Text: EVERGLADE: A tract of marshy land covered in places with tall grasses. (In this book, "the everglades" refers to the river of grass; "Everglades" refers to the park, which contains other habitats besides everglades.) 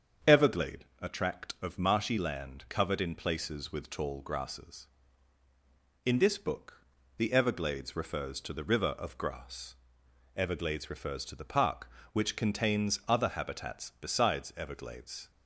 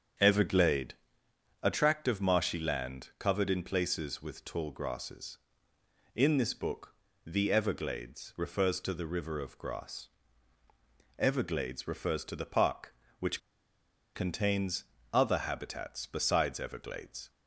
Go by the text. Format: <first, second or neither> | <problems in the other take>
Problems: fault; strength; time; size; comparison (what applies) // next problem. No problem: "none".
first | starts louder than the rest; strong; until 1.8 s; 7.5 dB; strong in the first // pauses between "which" and "contains"; noticeable; at 13.3 s; 0.76 s long // pauses between "contains" and "other"; slight; at 14.8 s; 0.30 s long